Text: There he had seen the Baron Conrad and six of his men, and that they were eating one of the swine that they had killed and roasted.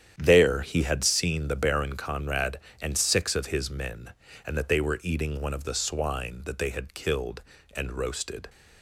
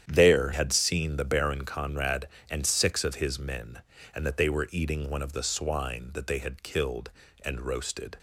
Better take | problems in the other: first | starts louder than the rest; strong; until 1.1 s; 9.5 dB; strong in the first // skips "he"; at 0.5 s

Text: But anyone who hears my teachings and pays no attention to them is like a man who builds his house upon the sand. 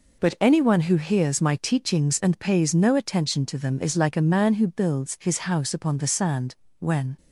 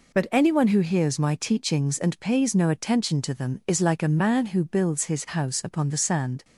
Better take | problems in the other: second | goes on to say "When"; slight; from 6.7 s on; 0.38 s long

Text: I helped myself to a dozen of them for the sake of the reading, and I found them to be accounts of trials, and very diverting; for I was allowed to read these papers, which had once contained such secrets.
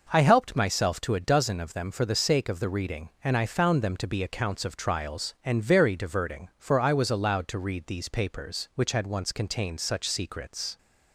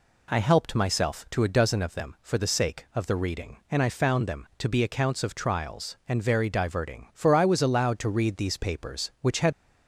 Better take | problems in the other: first | stops before "once contained such secrets"; at 9.5 s

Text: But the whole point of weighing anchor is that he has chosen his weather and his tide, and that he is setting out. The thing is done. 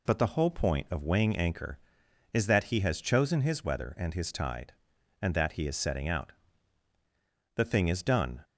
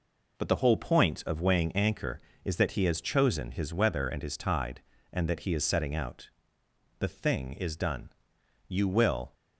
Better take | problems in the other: first | goes on to say "You will"; noticeable; from 8.6 s on; 0.66 s long

